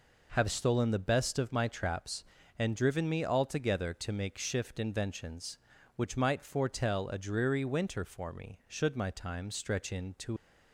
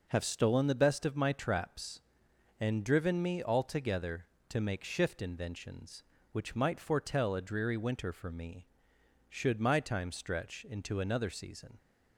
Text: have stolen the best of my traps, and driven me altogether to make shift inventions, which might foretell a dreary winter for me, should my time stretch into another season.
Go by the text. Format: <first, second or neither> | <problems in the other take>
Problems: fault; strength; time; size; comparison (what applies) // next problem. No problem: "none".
second | stops before "another season"; at 10.3 s